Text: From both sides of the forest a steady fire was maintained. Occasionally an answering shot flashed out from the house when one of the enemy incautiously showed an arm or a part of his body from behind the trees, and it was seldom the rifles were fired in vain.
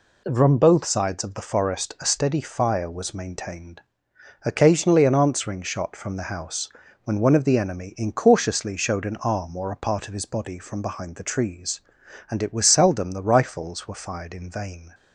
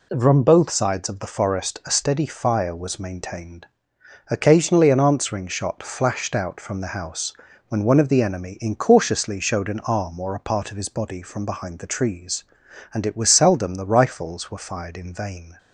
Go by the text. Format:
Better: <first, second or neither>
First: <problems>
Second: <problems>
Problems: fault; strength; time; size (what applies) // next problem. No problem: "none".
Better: second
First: skips "flashed out"; at 5.9 s // pauses between "house" and "when"; slight; at 6.7 s; 0.32 s long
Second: pauses between "house" and "when"; slight; at 7.3 s; 0.32 s long